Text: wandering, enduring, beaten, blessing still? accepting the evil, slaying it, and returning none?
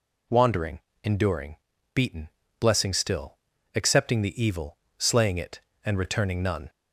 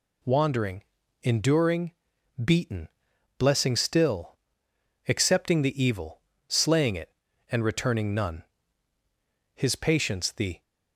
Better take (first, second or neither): first